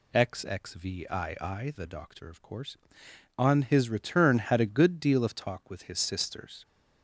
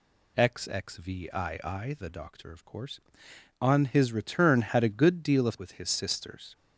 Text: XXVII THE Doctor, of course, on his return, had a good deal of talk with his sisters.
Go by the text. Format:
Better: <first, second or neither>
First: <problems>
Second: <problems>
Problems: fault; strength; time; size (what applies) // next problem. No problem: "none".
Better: first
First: none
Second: skips "talk"; at 5.5 s